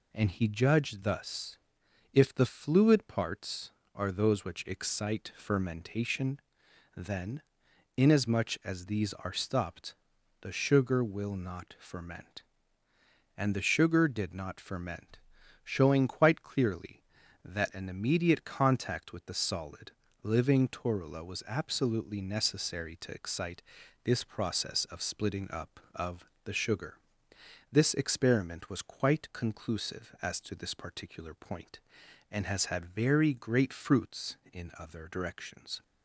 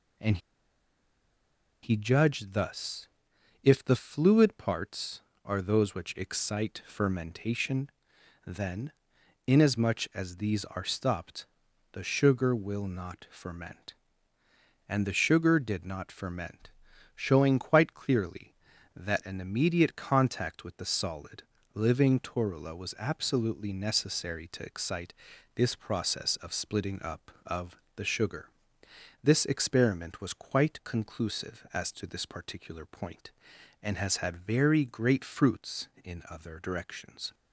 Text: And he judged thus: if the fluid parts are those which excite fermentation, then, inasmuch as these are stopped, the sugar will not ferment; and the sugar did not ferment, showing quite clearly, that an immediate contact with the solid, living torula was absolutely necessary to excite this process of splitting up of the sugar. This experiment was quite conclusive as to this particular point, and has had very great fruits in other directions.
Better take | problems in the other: first | pauses between "And" and "he"; strong; at 0.3 s; 1.4 s long // pauses between "excite" and "this"; at 25.1 s; 0.40 s long; also in the first // pauses between "of" and "the"; slight; at 27.7 s; 0.18 s long; slight in the first

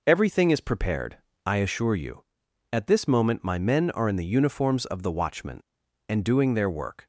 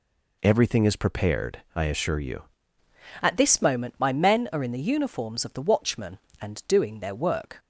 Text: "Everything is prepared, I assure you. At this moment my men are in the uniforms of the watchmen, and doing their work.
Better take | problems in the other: first | changes voice at "At"; from 3.2 s on; 4.3 s long

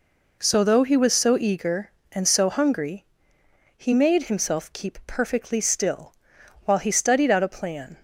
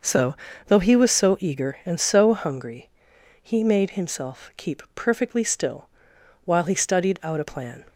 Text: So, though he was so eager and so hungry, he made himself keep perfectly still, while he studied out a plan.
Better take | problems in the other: neither | none

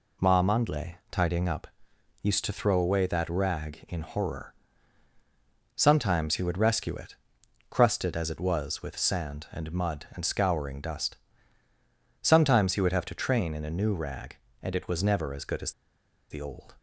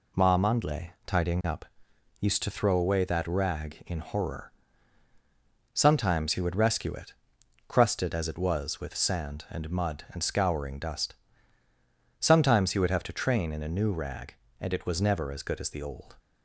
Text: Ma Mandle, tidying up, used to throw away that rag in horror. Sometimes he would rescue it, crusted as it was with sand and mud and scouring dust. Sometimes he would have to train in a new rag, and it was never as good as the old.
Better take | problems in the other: second | pauses between "as" and "the"; noticeable; at 15.7 s; 0.59 s long

